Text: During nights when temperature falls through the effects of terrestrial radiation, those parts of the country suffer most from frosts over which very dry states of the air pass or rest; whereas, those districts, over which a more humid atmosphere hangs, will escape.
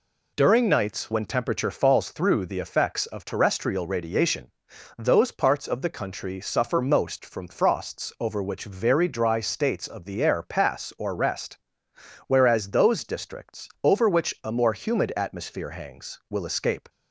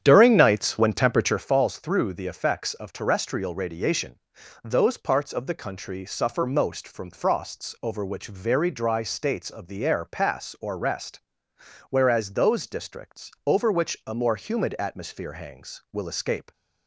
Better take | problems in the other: first | starts louder than the rest; strong; until 1.5 s; 9 dB

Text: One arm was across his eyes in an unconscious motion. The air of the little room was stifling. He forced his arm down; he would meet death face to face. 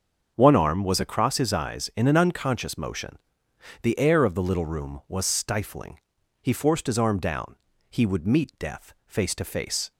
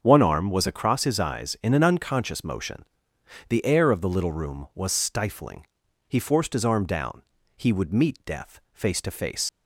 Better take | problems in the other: first | starts louder than the rest; until 1.0 s; 7 dB; also in the first // leaves "face" unfinished; at 9.4 s; 90 ms

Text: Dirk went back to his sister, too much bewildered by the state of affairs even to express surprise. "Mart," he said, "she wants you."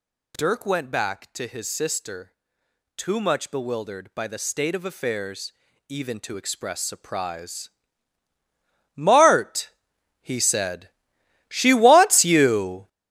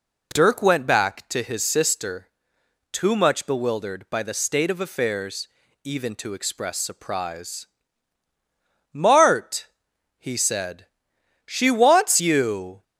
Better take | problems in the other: second | gets louder; strong; throughout; 9.5 dB // pauses between "affairs" and "even"; slight; at 5.5 s; 0.34 s long; slight in the second

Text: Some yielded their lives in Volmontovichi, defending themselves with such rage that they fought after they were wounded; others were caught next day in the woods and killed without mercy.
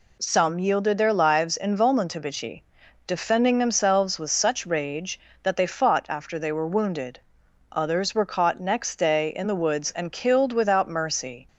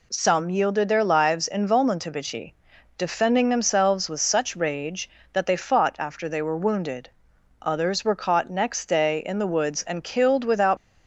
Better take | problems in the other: first | stops before "mercy"; at 10.7 s

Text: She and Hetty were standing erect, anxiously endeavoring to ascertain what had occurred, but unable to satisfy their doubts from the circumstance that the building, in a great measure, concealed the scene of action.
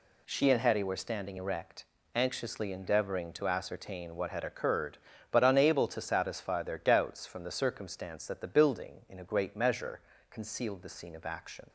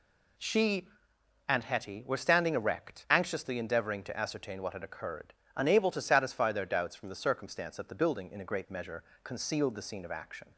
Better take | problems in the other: first | skips "but"; at 5.4 s

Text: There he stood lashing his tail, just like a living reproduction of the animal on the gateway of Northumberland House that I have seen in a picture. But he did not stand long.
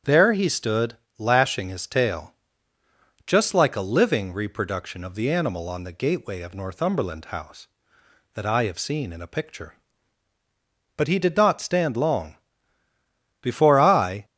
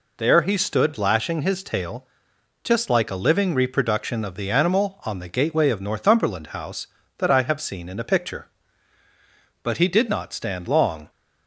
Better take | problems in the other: second | starts louder than the rest; strong; until 1.2 s; 8 dB // pauses between "stood" and "lashing"; slight; at 0.9 s; 0.20 s long // goes on to say "Before I"; noticeable; from 13.4 s on; 0.84 s long

